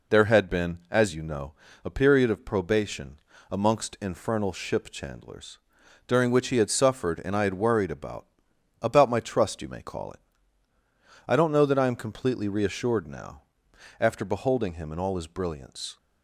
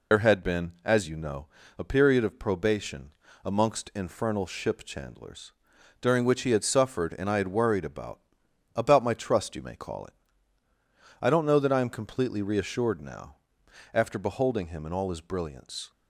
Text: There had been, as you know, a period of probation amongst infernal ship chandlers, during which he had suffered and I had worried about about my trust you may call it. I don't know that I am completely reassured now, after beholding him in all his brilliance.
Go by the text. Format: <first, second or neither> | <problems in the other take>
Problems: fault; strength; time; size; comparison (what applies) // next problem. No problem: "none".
first | loses the start of "There"; at 0.1 s; 65 ms // pauses between "probation" and "amongst"; slight; at 3.1 s; 0.32 s long; slight in the first // pauses between "about" and "about"; noticeable; at 8.2 s; 0.54 s long; noticeable in the first